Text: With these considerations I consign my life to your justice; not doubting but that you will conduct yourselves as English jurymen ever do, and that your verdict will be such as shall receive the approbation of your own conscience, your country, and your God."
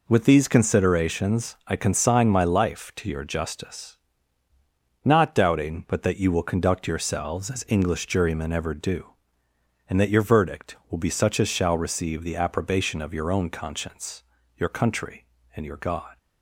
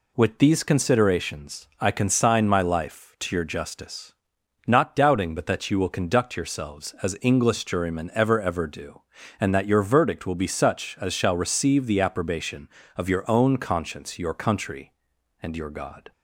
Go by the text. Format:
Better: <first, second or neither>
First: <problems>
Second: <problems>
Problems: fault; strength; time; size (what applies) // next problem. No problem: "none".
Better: first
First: none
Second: says "ever" twice; at 8.3 s